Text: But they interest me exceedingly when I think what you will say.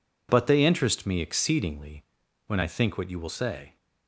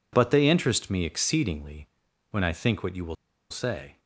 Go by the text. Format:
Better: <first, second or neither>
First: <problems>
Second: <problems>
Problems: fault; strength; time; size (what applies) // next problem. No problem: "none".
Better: first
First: pauses between "exceedingly" and "when"; at 2.0 s; 0.42 s long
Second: pauses between "exceedingly" and "when"; at 1.8 s; 0.42 s long // pauses between "will" and "say"; at 3.1 s; 0.37 s long